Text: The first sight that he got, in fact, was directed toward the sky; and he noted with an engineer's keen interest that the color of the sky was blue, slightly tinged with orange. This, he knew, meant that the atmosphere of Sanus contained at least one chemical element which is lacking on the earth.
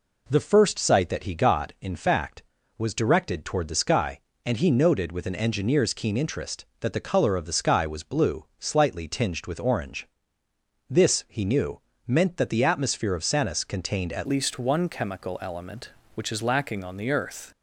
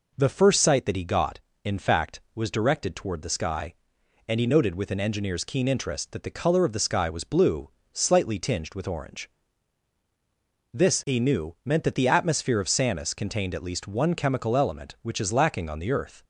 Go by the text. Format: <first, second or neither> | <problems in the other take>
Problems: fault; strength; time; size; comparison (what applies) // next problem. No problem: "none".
second | changes voice at "least"; from 14.2 s on; 3.2 s long